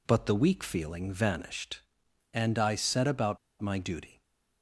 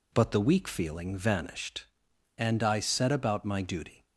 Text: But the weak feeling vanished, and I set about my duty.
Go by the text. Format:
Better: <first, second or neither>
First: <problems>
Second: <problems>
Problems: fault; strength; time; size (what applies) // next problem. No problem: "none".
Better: second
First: pauses between "about" and "my"; slight; at 3.3 s; 0.22 s long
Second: none